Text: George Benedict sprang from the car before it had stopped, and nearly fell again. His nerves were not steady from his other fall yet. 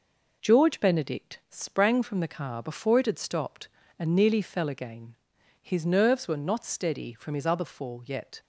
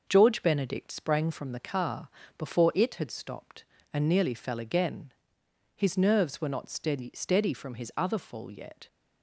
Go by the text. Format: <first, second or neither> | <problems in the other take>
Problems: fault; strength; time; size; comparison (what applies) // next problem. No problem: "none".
first | pauses between "car" and "before"; slight; at 2.0 s; 0.28 s long // says "steady" twice; at 7.1 s